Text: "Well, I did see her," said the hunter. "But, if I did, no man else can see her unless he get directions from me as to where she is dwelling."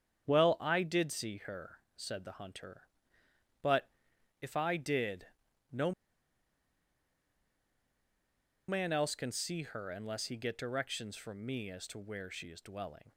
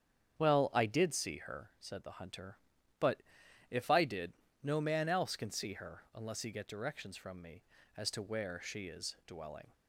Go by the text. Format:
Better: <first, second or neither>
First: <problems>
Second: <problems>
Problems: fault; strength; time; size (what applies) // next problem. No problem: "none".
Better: second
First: starts louder than the rest; strong; until 1.2 s; 8.5 dB // pauses between "no" and "man"; strong; at 5.9 s; 2.7 s long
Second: starts louder than the rest; strong; until 1.4 s; 8 dB